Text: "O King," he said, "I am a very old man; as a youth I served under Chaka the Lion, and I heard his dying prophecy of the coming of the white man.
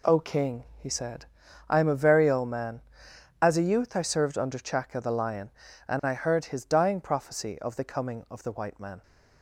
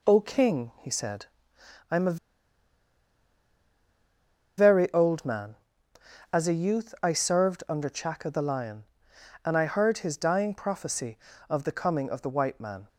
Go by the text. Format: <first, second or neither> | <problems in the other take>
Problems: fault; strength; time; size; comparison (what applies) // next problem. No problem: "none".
first | pauses between "a" and "very"; strong; at 2.1 s; 2.3 s long